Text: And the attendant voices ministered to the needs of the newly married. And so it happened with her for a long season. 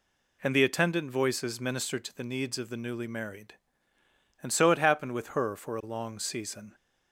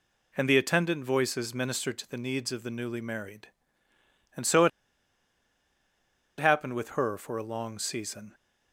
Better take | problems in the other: first | pauses between "it" and "happened"; strong; at 4.7 s; 1.7 s long

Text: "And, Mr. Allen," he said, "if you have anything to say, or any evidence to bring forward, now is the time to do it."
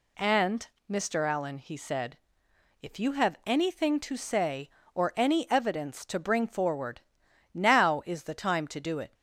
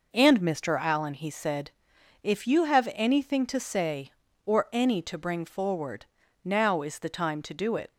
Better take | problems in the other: first | skips "evidence"; at 5.0 s

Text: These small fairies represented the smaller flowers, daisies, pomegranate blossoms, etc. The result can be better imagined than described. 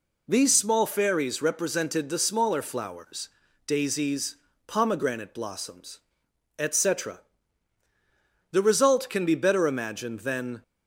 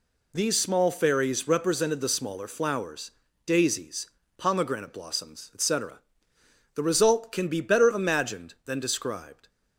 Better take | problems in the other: second | stops before "described"; at 10.6 s

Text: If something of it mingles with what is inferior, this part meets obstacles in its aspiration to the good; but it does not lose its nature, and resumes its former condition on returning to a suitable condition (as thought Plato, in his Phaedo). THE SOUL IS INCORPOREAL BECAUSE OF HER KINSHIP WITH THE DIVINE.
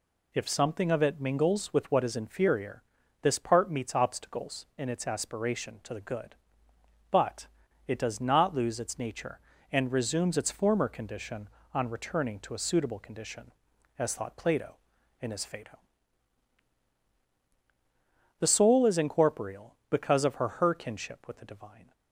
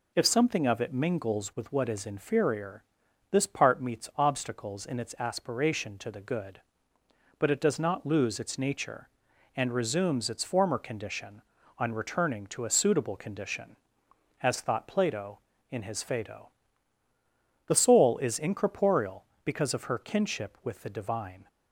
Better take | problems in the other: second | pauses between "but" and "it"; at 7.4 s; 0.37 s long // says "HER" twice; at 20.5 s

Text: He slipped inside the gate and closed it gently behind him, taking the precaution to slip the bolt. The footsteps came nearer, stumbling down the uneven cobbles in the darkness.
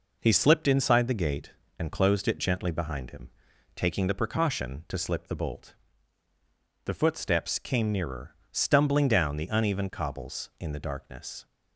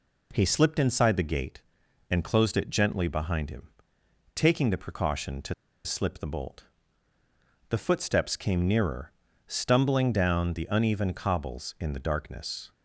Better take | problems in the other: first | pauses between "to" and "slip"; slight; at 5.5 s; 0.31 s long

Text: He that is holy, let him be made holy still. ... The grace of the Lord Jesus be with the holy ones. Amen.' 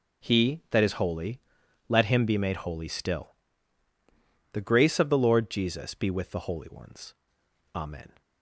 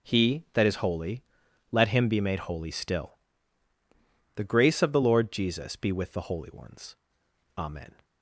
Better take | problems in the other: neither | none

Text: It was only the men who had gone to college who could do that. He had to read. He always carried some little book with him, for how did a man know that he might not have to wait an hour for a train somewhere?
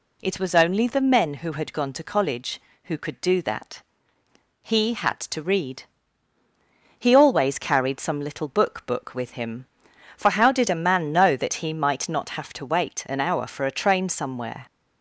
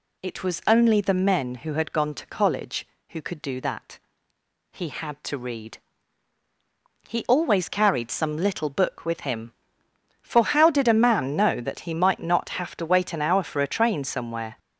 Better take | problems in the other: second | says "book" twice; at 8.8 s

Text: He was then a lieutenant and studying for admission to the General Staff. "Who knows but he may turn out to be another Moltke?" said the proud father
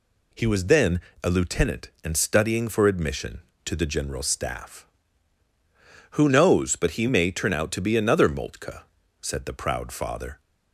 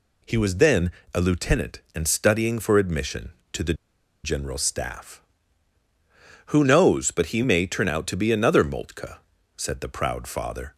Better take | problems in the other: first | pauses between "then" and "a"; slight; at 0.9 s; 0.22 s long; slight in the first // pauses between "the" and "General"; noticeable; at 3.7 s; 0.49 s long

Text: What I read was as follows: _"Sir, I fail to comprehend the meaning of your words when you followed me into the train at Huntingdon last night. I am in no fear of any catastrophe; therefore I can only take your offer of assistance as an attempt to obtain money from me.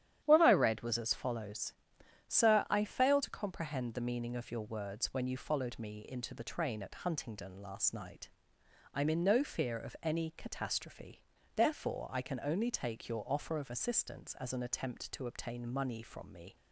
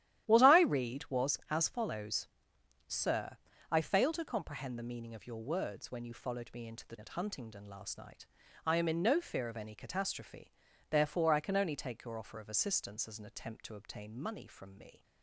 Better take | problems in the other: first | starts louder than the rest; strong; until 1.3 s; 12.5 dB; strong in the first // skips "train"; at 6.9 s

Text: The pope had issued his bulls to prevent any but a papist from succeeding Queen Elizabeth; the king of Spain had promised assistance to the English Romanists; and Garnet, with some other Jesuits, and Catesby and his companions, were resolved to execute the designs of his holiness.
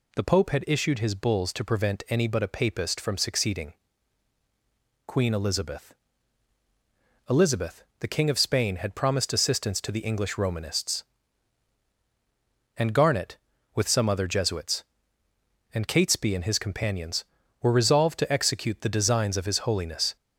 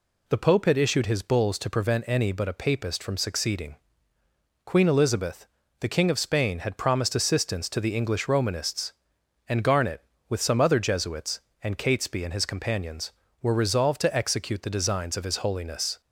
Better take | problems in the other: second | pauses between "succeeding" and "Queen"; strong; at 3.7 s; 1.3 s long; noticeable in the second // says "Elizabeth" twice; at 7.2 s

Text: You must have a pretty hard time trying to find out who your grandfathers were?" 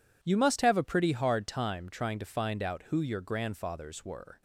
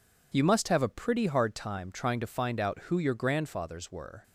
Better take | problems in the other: neither | none

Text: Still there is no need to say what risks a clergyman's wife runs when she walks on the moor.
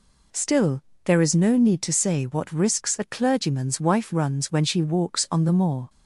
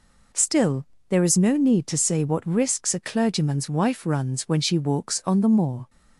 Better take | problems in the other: neither | pauses between "Still" and "there"; slight; the same in both

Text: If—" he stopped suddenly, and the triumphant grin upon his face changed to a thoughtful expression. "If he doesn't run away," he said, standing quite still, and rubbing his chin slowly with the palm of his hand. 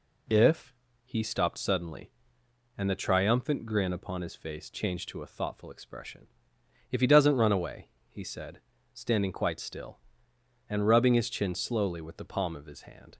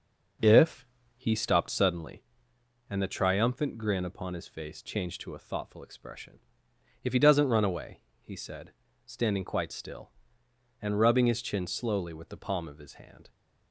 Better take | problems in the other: first | starts louder than the rest; noticeable; until 2.1 s; 5.5 dB

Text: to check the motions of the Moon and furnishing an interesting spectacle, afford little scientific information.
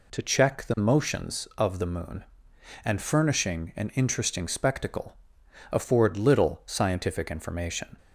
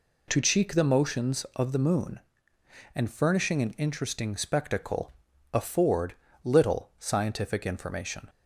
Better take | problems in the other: first | says "cheek" for "check"; at 0.4 s // pauses between "afford" and "little"; slight; at 6.1 s; 0.30 s long

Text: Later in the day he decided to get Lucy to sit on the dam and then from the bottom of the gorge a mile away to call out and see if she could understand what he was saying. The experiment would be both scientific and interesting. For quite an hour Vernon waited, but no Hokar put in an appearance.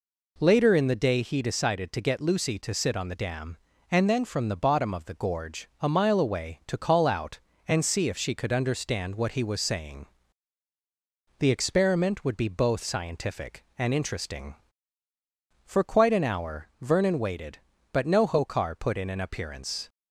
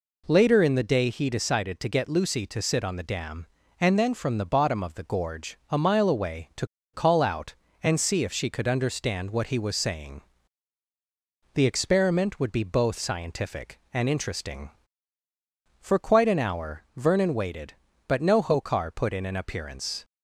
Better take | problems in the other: first | pauses between "to" and "call"; slight; at 6.6 s; 0.28 s long

